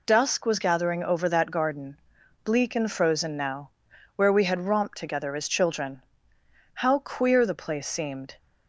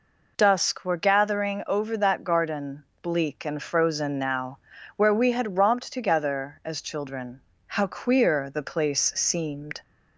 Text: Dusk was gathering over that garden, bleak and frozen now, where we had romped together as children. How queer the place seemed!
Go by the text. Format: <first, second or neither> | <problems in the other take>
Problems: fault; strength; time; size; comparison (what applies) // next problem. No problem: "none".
first | says "were" for "was"; at 0.8 s